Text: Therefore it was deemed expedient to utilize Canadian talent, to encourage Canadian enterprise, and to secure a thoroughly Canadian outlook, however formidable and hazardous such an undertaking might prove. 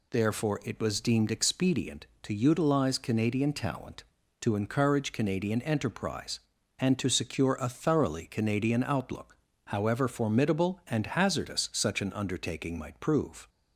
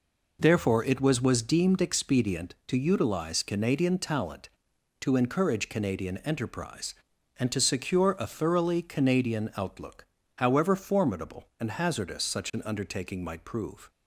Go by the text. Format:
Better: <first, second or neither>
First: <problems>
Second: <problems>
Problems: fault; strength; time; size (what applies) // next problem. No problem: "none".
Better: first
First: none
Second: says "was" twice; at 1.2 s